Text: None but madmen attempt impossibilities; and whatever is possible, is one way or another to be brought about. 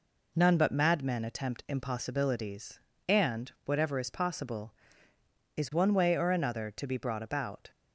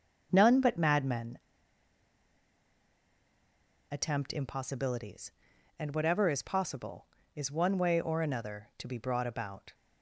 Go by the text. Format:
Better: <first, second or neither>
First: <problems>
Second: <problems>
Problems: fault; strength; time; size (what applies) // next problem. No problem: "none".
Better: first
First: none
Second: starts louder than the rest; until 1.3 s; 7 dB // pauses between "madmen" and "attempt"; strong; at 1.3 s; 2.5 s long